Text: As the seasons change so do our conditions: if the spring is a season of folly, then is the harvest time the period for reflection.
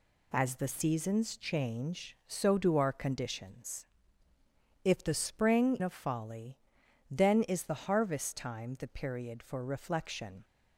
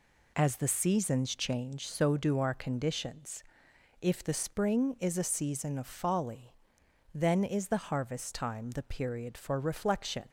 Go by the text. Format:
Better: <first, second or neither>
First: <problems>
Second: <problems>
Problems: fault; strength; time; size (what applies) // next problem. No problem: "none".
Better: second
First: skips "is a season"; at 5.7 s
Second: none